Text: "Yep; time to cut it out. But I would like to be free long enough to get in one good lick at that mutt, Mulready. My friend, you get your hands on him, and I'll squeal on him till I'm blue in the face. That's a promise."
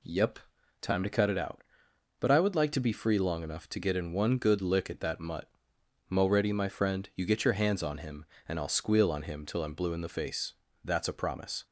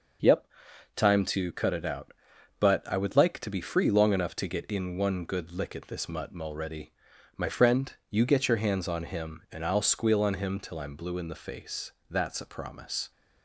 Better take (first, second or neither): first